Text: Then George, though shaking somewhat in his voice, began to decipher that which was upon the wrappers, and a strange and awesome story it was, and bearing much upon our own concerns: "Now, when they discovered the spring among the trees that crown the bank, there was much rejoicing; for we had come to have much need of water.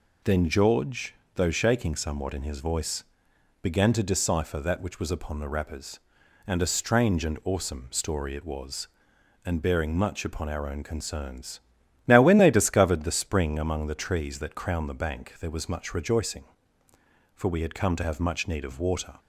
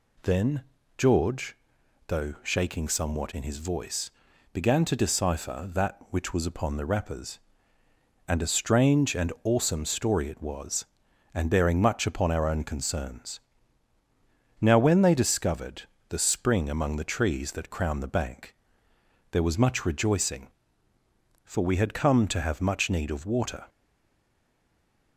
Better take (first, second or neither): first